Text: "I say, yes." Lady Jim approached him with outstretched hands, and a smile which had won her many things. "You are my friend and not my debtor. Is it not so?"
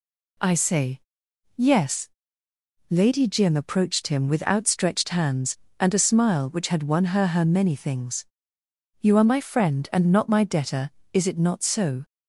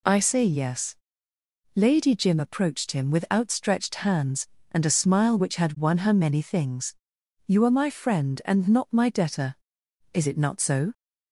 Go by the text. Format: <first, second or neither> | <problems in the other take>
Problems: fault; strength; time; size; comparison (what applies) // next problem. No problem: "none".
second | says "her" twice; at 7.2 s